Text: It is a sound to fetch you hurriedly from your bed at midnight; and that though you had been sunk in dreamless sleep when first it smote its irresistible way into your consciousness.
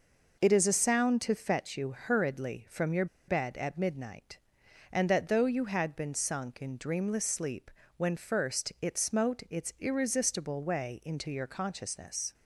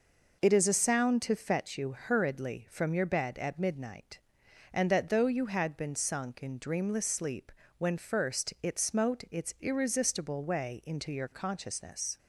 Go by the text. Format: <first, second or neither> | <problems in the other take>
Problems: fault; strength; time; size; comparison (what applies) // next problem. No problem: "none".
second | pauses between "your" and "bed"; slight; at 3.0 s; 0.22 s long // pauses between "sleep" and "when"; slight; at 7.6 s; 0.28 s long; slight in the second